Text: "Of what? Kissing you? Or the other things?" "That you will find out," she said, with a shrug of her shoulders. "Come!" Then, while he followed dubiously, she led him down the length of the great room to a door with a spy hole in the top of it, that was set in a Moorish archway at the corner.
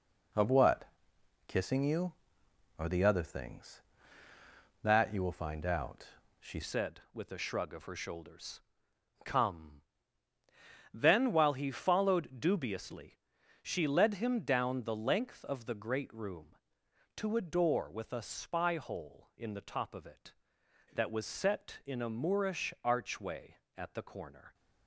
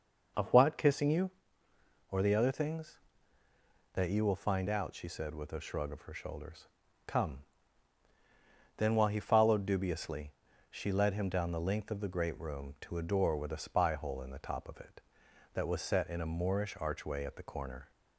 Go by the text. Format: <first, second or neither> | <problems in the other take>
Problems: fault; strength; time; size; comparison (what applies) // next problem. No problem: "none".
second | changes voice at "said"; from 6.6 s on; 17.9 s long